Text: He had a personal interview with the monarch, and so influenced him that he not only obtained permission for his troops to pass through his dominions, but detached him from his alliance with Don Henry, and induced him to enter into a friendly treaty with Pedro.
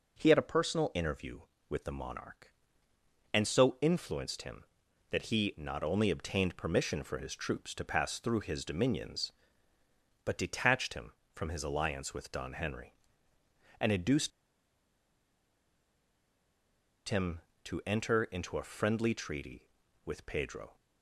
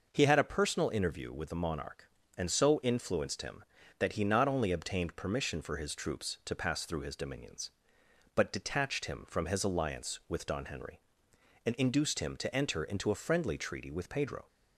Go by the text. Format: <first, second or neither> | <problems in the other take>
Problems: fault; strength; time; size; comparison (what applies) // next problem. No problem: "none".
second | pauses between "induced" and "him"; strong; at 14.3 s; 2.7 s long